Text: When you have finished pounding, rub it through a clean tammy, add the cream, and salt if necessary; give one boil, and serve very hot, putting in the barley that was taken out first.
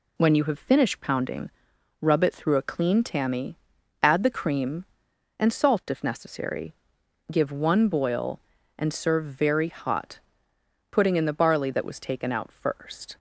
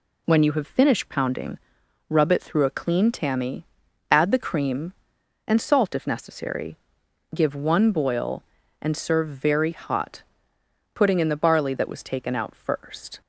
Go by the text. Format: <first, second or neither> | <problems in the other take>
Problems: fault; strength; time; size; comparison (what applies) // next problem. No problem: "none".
neither | none